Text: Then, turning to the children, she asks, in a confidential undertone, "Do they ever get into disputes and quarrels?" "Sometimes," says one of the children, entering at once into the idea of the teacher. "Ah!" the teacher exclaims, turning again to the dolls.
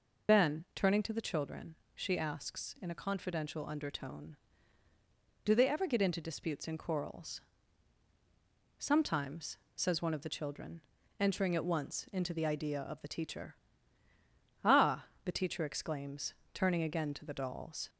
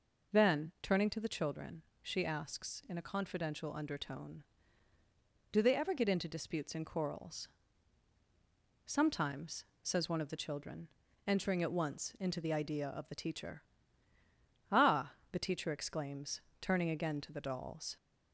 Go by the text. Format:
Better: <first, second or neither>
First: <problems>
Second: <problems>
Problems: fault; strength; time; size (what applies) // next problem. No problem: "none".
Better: second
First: loses the start of "Then"; at 0.2 s; 40 ms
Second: none